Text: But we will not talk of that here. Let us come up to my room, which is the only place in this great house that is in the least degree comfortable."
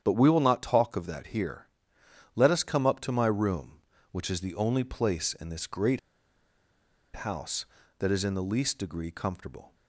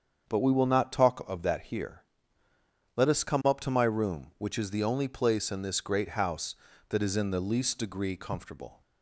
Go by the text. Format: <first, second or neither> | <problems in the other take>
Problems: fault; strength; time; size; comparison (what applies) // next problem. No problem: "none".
second | starts louder than the rest; strong; until 1.0 s; 9 dB; strong in the second // pauses between "great" and "house"; at 5.9 s; 1.1 s long